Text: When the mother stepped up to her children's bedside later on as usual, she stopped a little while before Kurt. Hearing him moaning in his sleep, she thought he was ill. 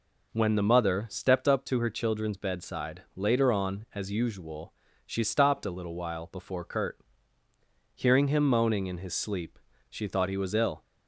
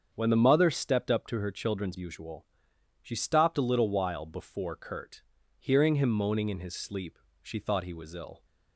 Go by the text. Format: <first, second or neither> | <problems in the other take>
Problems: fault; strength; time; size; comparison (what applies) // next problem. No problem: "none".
first | starts louder than the rest; strong; until 1.1 s; 7 dB // skips "bedside later on as"; at 1.9 s